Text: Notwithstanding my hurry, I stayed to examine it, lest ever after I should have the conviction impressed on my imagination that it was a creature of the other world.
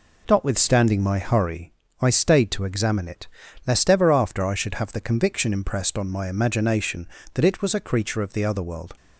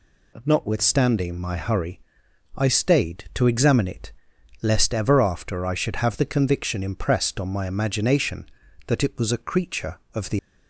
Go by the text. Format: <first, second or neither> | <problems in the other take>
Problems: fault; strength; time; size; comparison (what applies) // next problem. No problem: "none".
first | stops before "other world"; at 10.3 s